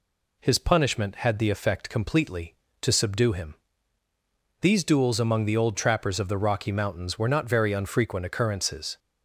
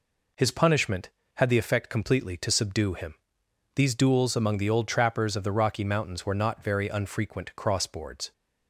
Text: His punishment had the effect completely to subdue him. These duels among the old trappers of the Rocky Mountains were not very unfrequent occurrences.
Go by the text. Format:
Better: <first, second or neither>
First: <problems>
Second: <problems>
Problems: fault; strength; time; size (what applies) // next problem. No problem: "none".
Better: first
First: none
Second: says "crossboards" for "occurrences"; at 7.5 s